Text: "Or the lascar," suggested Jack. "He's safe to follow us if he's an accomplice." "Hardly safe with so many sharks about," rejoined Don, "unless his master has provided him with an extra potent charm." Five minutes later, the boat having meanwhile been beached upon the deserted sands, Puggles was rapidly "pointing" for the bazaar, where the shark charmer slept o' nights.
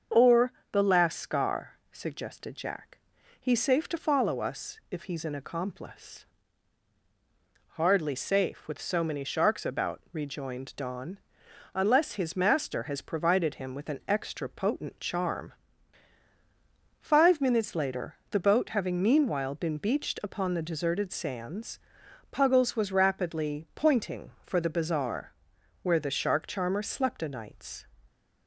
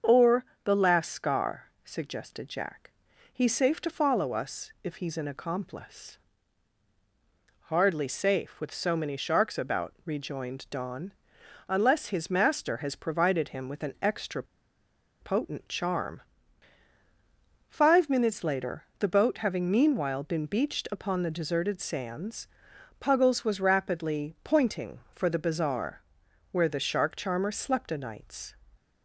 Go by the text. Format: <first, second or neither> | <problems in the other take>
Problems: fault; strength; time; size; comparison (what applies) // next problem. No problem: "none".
first | starts louder than the rest; until 1.2 s; 6.5 dB; also in the first // pauses between "Or" and "the"; slight; at 0.4 s; 0.20 s long; slight in the first // pauses between "extra" and "potent"; noticeable; at 14.4 s; 0.77 s long